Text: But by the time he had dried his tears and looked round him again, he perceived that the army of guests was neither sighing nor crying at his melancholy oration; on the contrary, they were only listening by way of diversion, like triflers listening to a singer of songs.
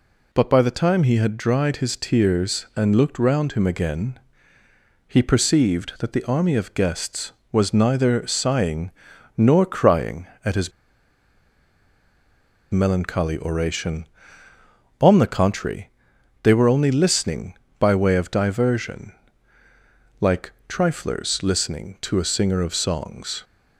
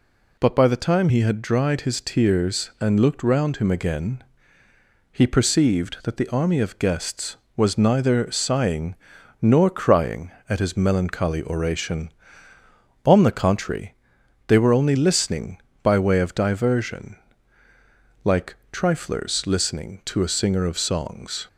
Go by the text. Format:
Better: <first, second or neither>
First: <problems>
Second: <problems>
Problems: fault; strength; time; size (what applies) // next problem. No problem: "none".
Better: second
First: pauses between "sighing" and "nor"; at 8.9 s; 0.44 s long // pauses between "his" and "melancholy"; strong; at 10.7 s; 2.0 s long // pauses between "like" and "triflers"; slight; at 20.5 s; 0.16 s long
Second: pauses between "sighing" and "nor"; at 8.9 s; 0.44 s long // pauses between "like" and "triflers"; slight; at 18.5 s; 0.16 s long